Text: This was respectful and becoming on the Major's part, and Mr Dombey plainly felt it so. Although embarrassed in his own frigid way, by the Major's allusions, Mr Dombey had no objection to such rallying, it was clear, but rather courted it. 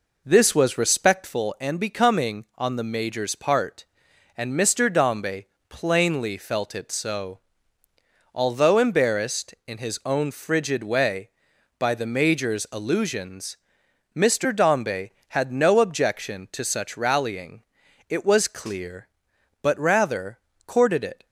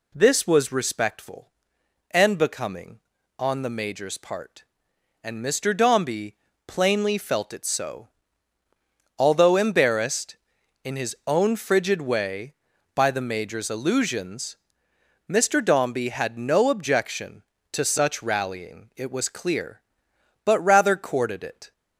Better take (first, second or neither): second